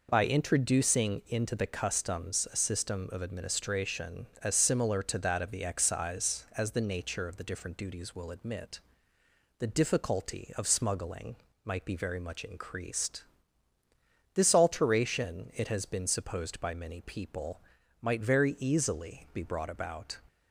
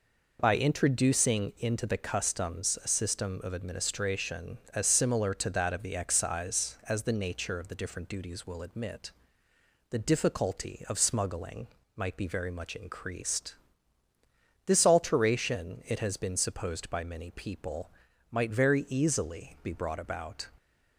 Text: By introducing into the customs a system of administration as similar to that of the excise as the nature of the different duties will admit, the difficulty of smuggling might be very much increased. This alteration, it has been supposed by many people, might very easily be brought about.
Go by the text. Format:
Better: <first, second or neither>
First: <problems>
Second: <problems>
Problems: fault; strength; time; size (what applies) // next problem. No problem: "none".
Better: neither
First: pauses between "smuggling" and "might"; slight; at 11.3 s; 0.28 s long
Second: pauses between "smuggling" and "might"; slight; at 11.6 s; 0.28 s long